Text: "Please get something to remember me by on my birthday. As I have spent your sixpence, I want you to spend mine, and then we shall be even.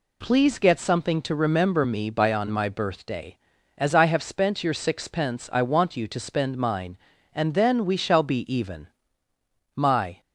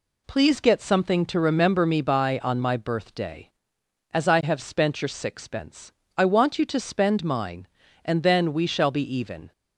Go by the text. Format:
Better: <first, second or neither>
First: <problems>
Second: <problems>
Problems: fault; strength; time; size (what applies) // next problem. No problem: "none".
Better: second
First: goes on to say "My"; slight; from 9.7 s on; 0.46 s long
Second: none